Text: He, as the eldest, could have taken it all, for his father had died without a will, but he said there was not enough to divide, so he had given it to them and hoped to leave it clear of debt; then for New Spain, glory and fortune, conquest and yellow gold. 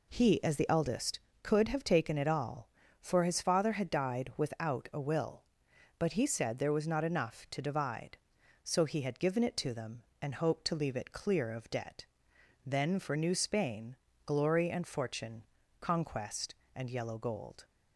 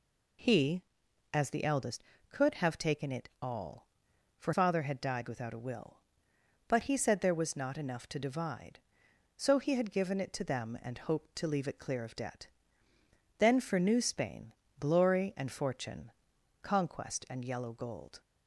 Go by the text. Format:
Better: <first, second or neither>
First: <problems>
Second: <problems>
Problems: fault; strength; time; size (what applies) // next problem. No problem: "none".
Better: first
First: none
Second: skips "his"; at 4.5 s